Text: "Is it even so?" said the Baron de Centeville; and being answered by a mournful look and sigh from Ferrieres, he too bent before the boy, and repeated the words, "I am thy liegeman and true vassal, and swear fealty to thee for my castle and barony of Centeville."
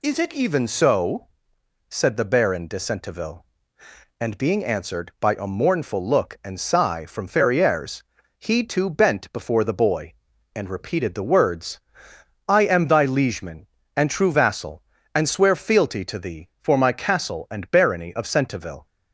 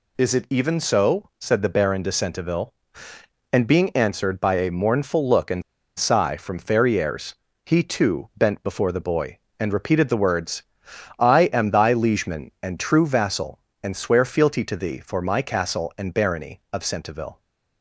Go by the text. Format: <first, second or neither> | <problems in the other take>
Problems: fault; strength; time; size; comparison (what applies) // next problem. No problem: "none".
first | pauses between "and" and "sigh"; at 5.6 s; 0.37 s long